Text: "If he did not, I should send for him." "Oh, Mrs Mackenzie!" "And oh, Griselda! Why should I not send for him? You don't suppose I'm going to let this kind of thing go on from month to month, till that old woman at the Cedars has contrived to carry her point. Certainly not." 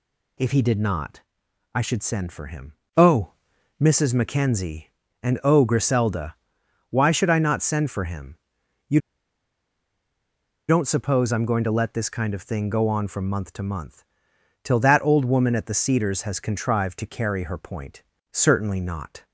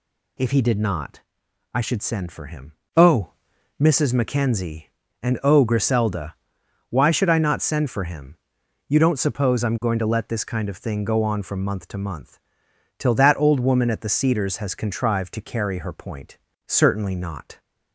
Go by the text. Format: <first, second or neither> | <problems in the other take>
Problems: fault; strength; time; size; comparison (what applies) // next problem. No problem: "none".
second | pauses between "You" and "don't"; strong; at 9.0 s; 1.6 s long